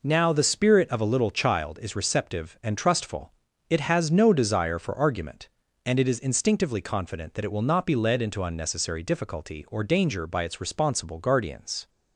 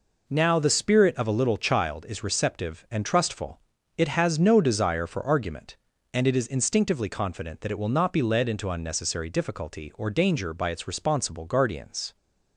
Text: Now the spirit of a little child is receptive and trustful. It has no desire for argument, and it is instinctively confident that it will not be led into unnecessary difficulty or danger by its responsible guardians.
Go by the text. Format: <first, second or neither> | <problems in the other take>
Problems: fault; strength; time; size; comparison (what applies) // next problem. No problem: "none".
neither | none